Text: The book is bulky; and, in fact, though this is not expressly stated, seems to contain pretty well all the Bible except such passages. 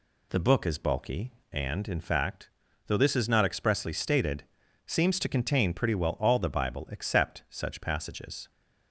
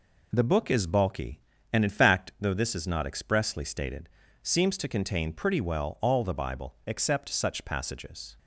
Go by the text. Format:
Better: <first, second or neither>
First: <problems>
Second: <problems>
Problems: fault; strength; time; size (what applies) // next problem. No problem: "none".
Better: neither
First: none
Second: none